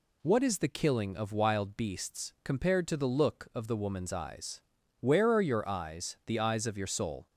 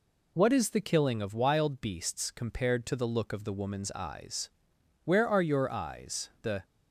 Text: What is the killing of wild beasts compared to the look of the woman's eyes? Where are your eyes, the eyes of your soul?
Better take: first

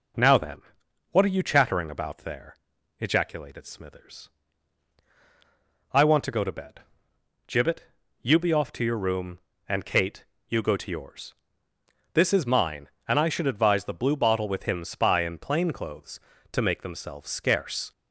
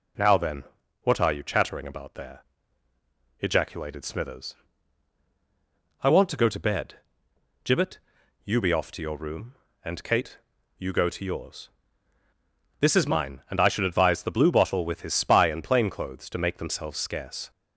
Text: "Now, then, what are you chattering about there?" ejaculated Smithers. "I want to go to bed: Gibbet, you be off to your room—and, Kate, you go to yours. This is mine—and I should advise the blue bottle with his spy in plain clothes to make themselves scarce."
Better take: second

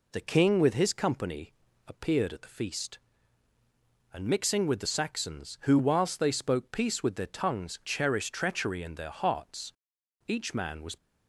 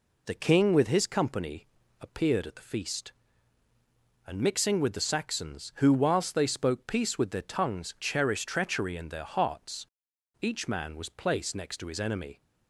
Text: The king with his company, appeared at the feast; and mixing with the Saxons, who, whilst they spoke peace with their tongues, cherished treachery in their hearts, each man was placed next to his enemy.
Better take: second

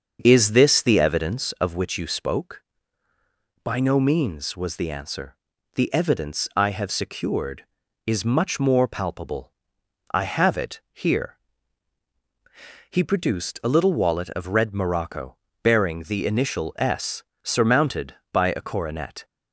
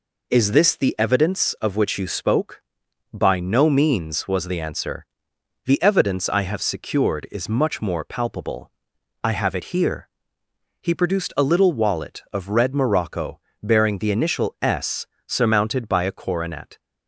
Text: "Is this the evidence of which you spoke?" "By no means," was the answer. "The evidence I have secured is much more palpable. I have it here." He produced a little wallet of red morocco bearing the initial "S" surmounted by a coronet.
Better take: second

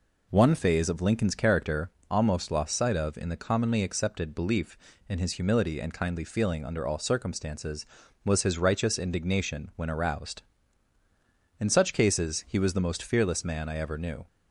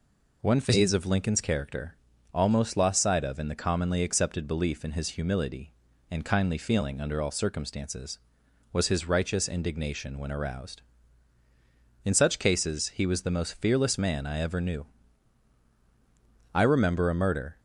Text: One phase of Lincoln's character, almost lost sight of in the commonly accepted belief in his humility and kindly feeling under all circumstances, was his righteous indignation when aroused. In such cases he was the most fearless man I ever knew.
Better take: first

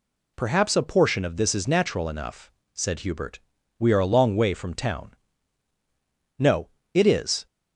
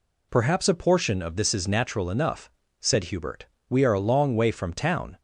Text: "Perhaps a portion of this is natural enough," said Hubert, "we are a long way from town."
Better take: second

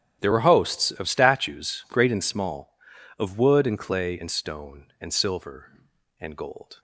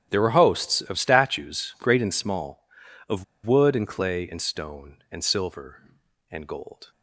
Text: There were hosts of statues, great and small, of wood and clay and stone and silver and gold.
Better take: first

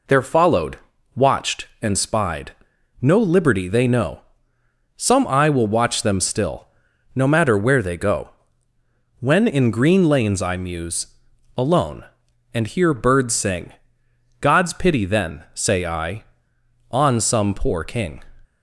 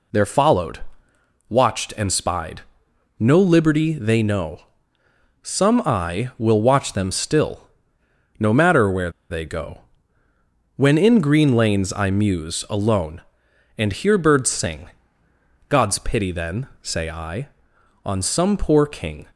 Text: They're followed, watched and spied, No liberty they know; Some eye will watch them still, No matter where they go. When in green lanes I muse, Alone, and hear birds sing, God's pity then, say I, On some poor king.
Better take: first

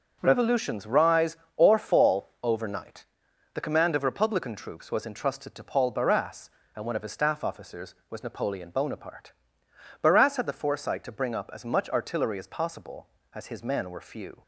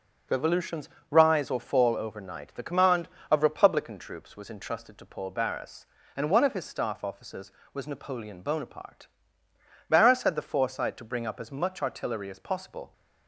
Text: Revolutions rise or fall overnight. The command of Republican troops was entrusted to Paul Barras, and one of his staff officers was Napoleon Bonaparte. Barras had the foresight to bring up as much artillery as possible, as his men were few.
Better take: first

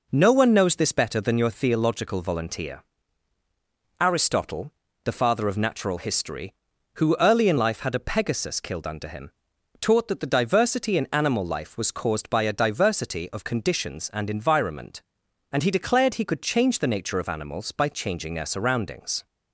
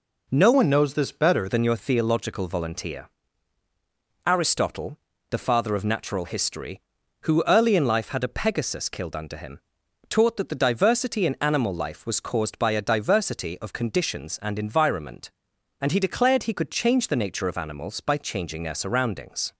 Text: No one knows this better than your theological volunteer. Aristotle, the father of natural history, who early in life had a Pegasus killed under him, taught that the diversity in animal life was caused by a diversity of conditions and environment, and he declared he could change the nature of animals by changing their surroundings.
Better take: first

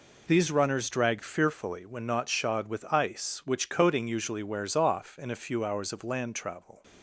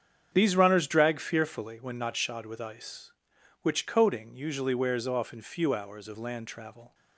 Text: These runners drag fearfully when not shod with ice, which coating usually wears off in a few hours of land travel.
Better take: first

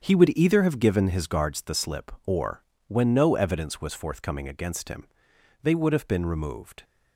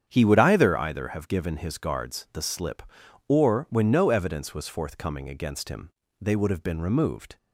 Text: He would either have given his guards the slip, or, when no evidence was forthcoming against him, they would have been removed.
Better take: first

